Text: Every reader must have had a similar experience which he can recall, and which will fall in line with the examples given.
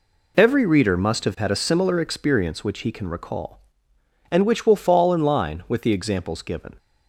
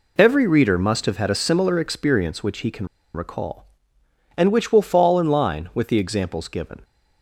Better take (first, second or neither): first